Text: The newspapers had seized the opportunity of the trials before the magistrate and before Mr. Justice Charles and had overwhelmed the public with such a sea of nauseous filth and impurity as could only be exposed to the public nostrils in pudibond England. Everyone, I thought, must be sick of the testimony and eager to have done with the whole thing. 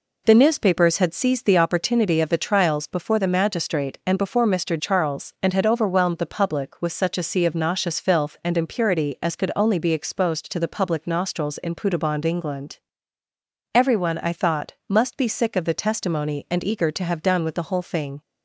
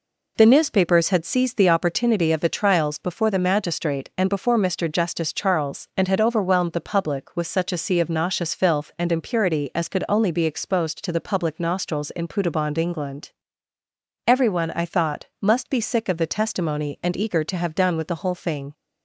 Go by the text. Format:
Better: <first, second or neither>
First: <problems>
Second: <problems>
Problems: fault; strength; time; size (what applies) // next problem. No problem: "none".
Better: second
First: skips "Justice"; at 4.7 s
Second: none